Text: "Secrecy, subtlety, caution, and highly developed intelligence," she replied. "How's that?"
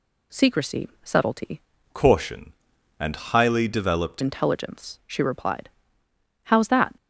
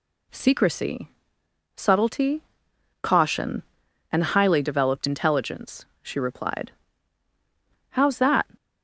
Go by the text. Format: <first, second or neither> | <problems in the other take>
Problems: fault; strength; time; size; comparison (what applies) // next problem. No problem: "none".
second | changes voice from "caution" to "developed"; from 1.9 to 4.2 s; 2.3 s long